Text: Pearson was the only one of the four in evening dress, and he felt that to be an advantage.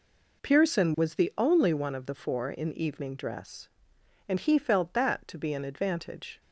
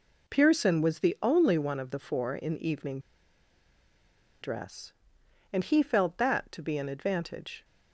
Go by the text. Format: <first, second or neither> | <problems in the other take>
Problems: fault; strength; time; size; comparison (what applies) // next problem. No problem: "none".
first | pauses between "evening" and "dress"; strong; at 2.9 s; 1.4 s long